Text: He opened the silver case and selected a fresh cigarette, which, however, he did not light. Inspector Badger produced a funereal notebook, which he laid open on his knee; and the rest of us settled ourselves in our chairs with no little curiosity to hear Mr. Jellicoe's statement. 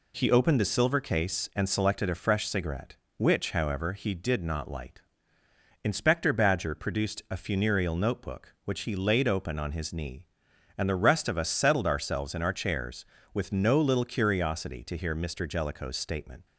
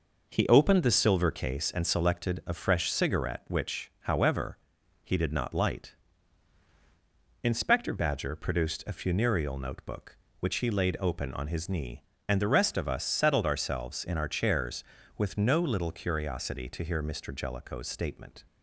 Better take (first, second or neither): neither